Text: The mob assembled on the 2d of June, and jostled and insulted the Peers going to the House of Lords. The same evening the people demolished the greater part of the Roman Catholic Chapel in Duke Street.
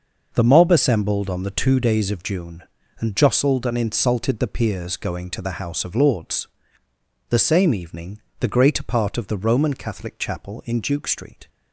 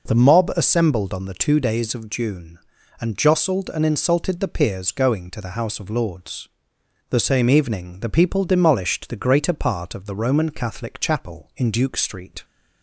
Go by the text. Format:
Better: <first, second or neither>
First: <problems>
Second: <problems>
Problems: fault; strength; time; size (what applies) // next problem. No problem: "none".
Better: second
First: pauses between "evening" and "the"; slight; at 8.2 s; 0.18 s long // skips "people demolished the"; at 8.4 s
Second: none